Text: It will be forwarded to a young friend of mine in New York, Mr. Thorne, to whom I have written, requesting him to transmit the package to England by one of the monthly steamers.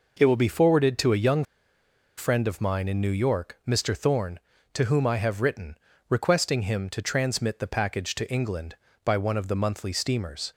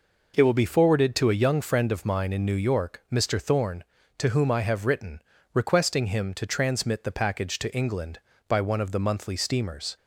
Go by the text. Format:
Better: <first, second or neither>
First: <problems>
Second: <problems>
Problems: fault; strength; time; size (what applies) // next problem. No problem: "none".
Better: second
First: pauses between "young" and "friend"; noticeable; at 1.4 s; 0.74 s long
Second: none